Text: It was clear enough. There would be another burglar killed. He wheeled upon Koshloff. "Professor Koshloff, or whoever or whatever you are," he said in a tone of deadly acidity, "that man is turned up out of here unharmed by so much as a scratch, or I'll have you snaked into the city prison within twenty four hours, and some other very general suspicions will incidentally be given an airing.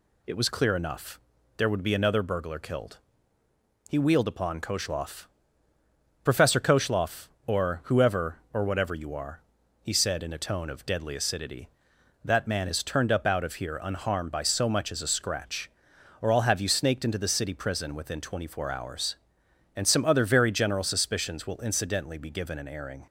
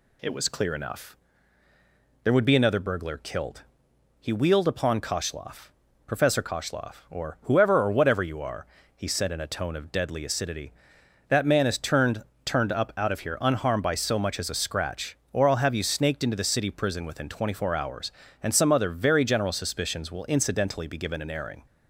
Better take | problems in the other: first | says "turned" twice; at 12.4 s

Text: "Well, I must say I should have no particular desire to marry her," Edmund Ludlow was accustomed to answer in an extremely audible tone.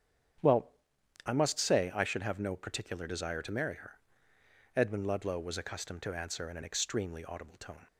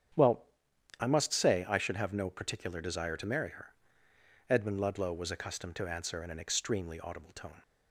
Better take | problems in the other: neither | starts louder than the rest; strong; the same in both

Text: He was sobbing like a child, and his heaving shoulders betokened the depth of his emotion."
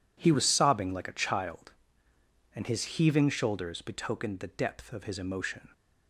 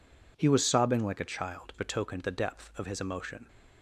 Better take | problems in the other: first | skips "and his heaving shoulders"; at 1.7 s

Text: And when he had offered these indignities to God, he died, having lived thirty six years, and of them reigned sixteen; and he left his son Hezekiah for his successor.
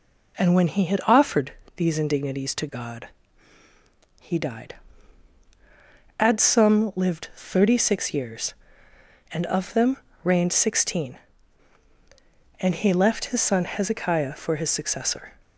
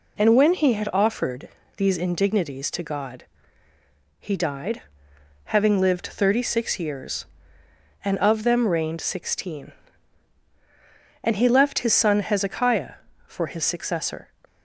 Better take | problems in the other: second | pauses between "offered" and "these"; slight; at 1.5 s; 0.24 s long; slight in the second // says "adsum" for "having"; at 6.1 s // pauses between "them" and "reigned"; slight; at 9.9 s; 0.28 s long

